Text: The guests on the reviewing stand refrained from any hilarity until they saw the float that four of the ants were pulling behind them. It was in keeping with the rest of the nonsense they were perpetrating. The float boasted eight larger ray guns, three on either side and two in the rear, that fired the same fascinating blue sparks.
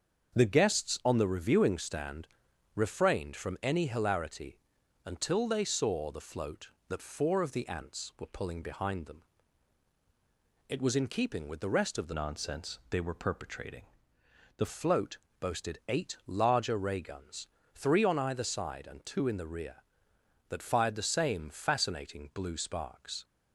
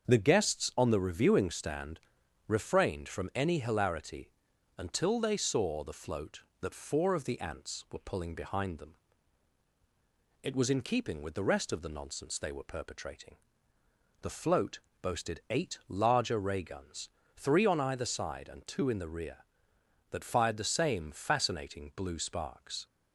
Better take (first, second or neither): second